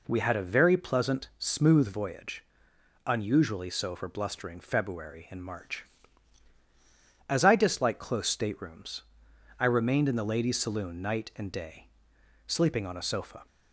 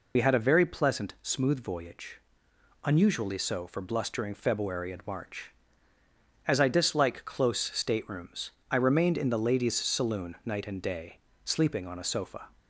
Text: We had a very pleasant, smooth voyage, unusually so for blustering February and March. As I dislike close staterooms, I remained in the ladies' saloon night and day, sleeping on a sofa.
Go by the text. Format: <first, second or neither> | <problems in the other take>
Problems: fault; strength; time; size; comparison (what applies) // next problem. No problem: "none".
first | loses the start of "We"; at 0.1 s; 70 ms